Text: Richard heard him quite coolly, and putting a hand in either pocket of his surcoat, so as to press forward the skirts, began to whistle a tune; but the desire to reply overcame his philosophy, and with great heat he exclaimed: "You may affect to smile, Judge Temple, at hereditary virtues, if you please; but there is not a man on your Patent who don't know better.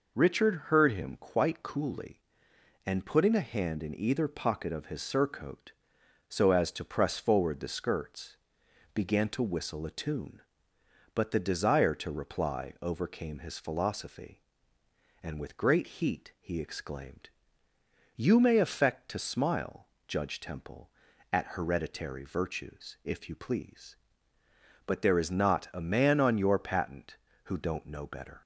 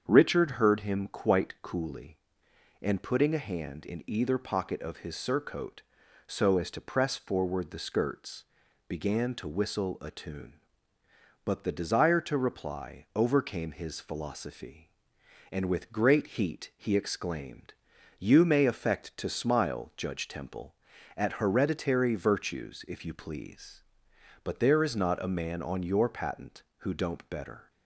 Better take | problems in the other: first | starts louder than the rest; strong; until 1.0 s; 7 dB // skips "know"; at 27.2 s

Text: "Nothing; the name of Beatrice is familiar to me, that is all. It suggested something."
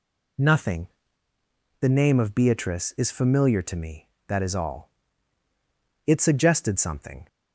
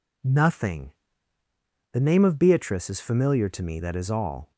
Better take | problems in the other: first | stops before "It suggested something"; at 4.5 s

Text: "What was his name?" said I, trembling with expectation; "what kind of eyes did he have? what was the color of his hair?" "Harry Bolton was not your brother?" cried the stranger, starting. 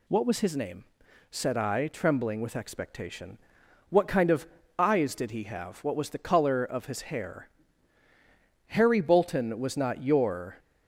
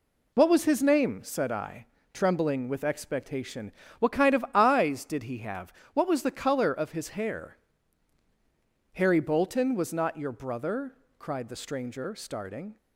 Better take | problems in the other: second | pauses between "of" and "eyes"; slight; at 4.4 s; 0.32 s long // stops before "brother cried the stranger starting"; at 10.5 s

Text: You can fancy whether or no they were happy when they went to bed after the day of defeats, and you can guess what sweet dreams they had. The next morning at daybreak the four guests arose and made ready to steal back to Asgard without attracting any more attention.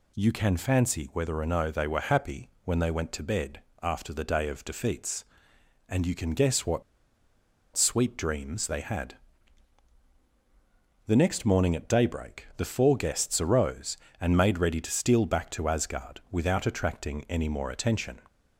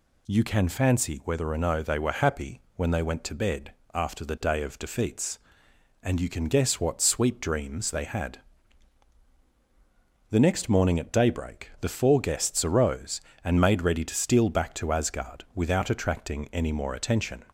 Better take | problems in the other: second | pauses between "happy" and "when"; slight; at 2.4 s; 0.16 s long; slight in the second // pauses between "bed" and "after"; slight; at 3.6 s; 0.20 s long; slight in the second // pauses between "what" and "sweet"; noticeable; at 6.8 s; 0.93 s long

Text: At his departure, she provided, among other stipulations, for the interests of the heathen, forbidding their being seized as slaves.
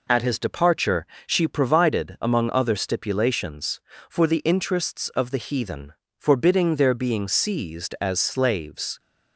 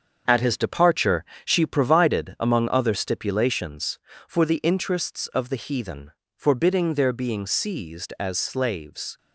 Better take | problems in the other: first | gets quieter; throughout; 7 dB

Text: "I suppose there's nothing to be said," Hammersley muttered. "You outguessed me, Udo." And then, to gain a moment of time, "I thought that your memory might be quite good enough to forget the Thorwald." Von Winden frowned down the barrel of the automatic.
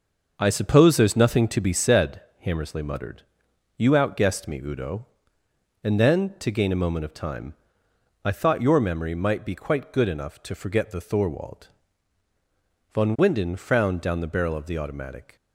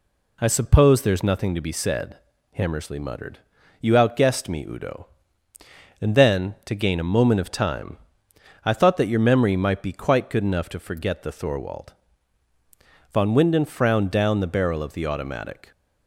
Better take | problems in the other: second | starts louder than the rest; until 1.3 s; 6 dB // skips "that"; at 8.6 s

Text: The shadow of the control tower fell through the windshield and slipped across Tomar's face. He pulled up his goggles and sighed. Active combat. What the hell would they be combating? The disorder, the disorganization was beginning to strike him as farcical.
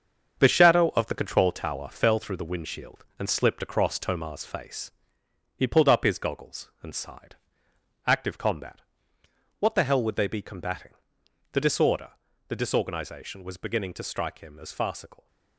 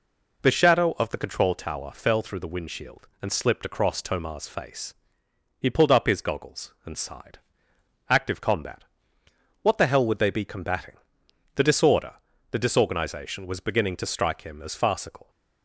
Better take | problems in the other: second | gets quieter; strong; throughout; 7.5 dB

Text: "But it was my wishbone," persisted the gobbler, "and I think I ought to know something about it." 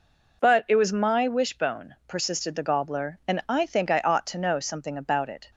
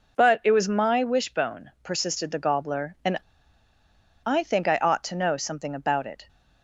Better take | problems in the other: first | pauses between "and" and "I"; at 3.1 s; 1.0 s long

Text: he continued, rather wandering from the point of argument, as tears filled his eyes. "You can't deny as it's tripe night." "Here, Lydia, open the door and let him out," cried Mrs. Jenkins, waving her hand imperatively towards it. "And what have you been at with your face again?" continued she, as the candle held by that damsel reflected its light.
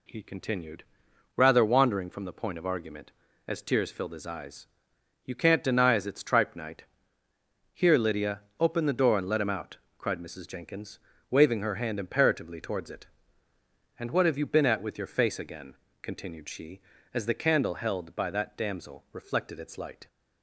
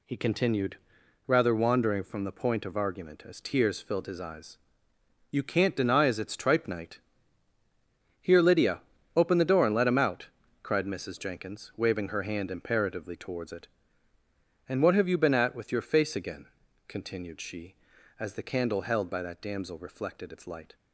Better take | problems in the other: neither | none

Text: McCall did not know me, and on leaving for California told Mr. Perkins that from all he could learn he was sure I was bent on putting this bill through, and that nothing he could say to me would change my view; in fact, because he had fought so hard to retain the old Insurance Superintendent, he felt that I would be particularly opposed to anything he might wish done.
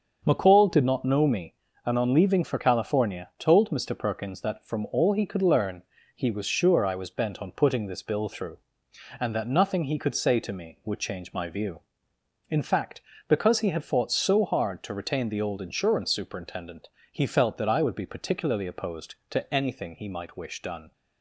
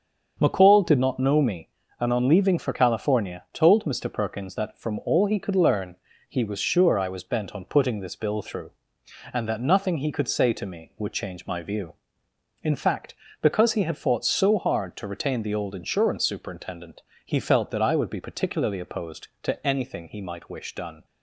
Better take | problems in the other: neither | starts louder than the rest; the same in both // pauses between "learn" and "he"; slight; the same in both

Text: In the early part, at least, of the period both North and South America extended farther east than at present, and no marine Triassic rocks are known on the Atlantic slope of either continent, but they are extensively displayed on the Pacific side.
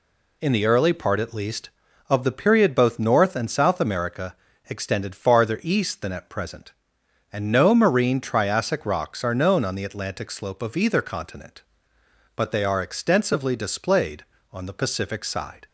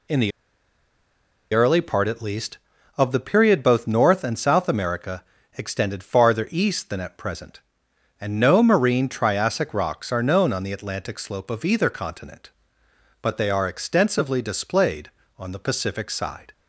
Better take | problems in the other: first | pauses between "the" and "early"; at 0.3 s; 1.2 s long // pauses between "America" and "extended"; slight; at 5.2 s; 0.32 s long; slight in the first

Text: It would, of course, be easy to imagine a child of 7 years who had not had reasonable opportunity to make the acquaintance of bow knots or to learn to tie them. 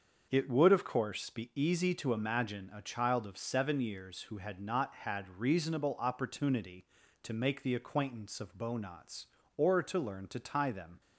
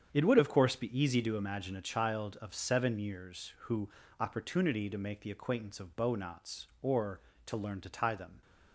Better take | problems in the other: first | starts louder than the rest; strong; until 1.1 s; 8 dB; also in the first // skips "had not had reasonable"; at 4.0 s

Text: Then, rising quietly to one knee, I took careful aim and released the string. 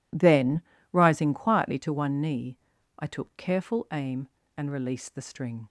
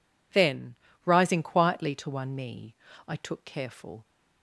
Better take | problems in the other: first | stops before "aim and released the string"; at 4.0 s

